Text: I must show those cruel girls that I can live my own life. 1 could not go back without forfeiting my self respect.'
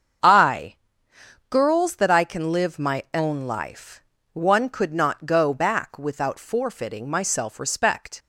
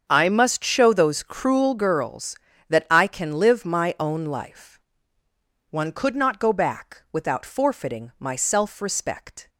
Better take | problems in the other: second | starts louder than the rest; until 1.9 s; 7 dB; also in the second // skips "must show those cruel"; at 1.1 s

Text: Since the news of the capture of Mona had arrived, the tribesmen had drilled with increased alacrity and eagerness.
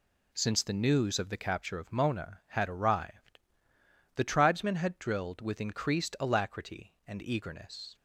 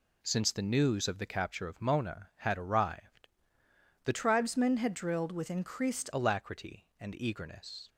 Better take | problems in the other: first | changes voice from "tribesmen" to "increased"; from 4.1 to 6.0 s; 1.9 s long

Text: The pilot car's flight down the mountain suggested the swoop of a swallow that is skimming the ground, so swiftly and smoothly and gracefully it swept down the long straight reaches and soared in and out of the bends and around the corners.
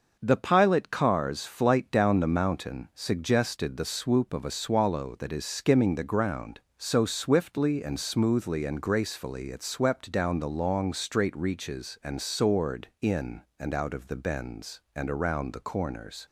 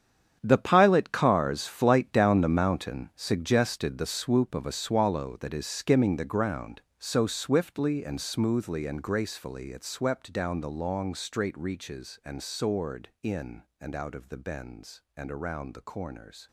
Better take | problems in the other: first | gets quieter; strong; throughout; 13 dB // starts louder than the rest; strong; until 1.4 s; 8.5 dB; noticeable in the first

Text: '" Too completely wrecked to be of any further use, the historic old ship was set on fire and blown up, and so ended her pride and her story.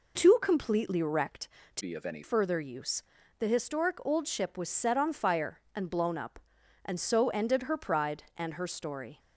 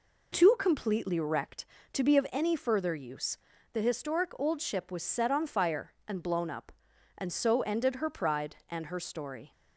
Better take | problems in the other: second | changes voice from "be" to "any"; from 1.7 to 2.2 s; 0.5 s long

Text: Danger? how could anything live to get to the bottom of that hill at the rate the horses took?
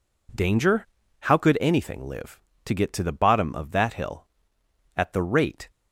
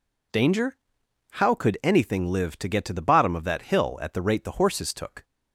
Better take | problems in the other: second | stops before "the horses took"; at 5.7 s

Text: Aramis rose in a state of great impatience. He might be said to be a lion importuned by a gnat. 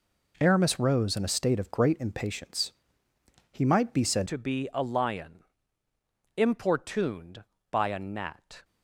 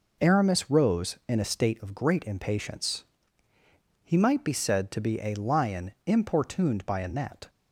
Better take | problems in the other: second | changes voice at "to"; from 4.2 s on; 4.4 s long // pauses between "lion" and "importuned"; noticeable; at 5.4 s; 0.92 s long

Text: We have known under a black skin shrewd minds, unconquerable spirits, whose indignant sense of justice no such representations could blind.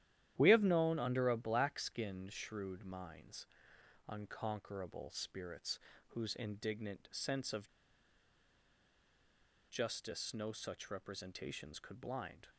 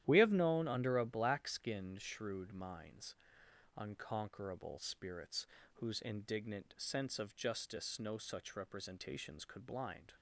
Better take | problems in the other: second | starts louder than the rest; strong; until 1.3 s; 12 dB; strong in the second // pauses between "of" and "justice"; strong; at 7.6 s; 2.0 s long

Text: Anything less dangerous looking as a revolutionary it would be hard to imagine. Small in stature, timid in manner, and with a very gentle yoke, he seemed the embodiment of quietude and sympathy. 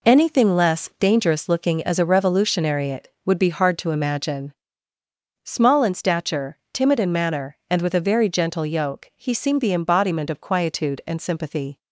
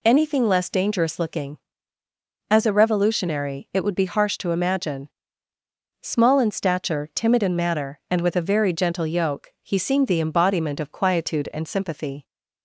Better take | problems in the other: first | says "harsh" for "hard"; at 4.0 s

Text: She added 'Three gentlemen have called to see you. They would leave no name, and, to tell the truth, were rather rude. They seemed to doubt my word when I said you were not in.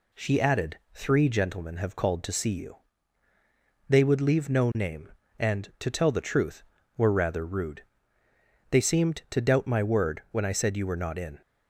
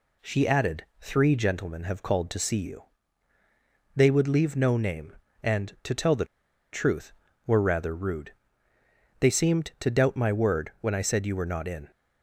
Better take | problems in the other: first | pauses between "the" and "truth"; noticeable; at 6.2 s; 0.47 s long

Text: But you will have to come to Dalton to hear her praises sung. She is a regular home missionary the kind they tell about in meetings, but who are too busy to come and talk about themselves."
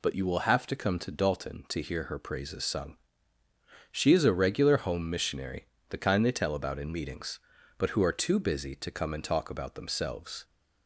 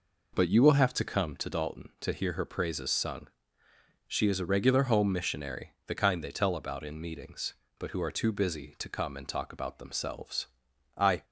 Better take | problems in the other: first | pauses between "missionary" and "the"; slight; at 5.7 s; 0.16 s long; slight in the first // goes on to say "I"; slight; from 10.9 s on; 0.28 s long

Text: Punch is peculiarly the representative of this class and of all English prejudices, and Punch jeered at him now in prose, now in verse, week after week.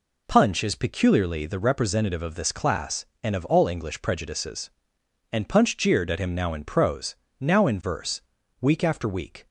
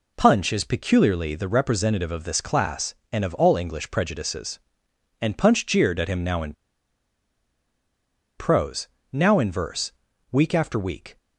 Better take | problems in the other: first | pauses between "in" and "prose"; strong; at 6.5 s; 1.8 s long

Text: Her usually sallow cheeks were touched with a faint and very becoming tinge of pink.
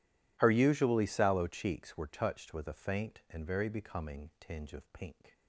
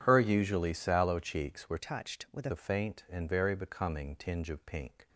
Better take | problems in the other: first | changes voice from "touched" to "with"; from 1.7 to 2.4 s; 0.7 s long

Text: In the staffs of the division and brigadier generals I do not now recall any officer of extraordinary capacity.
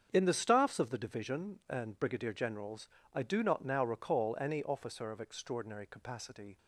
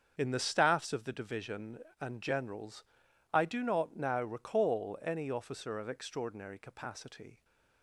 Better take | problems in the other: first | starts louder than the rest; strong; until 1.1 s; 7.5 dB; also in the first // skips "brigadier"; at 2.2 s // pauses between "generals" and "I"; noticeable; at 2.8 s; 0.48 s long; slight in the first

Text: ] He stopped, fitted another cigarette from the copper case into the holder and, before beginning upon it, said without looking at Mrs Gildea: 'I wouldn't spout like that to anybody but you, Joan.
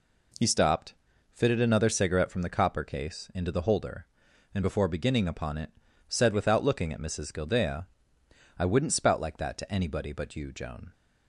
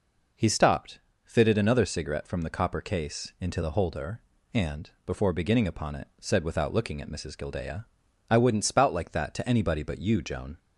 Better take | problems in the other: neither | none

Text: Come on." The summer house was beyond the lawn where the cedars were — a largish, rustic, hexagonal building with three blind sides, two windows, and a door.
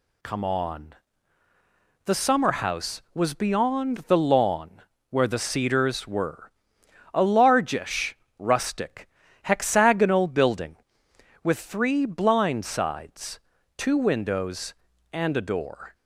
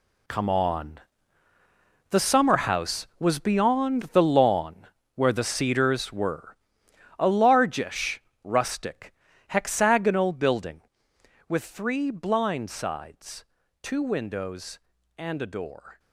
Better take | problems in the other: first | gets quieter; strong; throughout; 12 dB // pauses between "lawn" and "where"; slight; at 4.8 s; 0.28 s long; slight in the first

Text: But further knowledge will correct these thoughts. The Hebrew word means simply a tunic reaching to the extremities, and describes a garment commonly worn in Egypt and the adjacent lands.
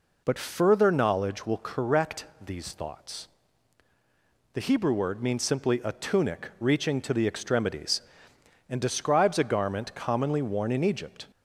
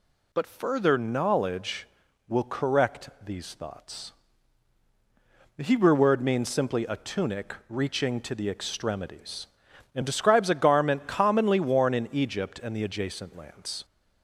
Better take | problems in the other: second | pauses between "correct" and "these"; slight; at 2.2 s; 0.18 s long // stops before "and the adjacent lands"; at 11.3 s

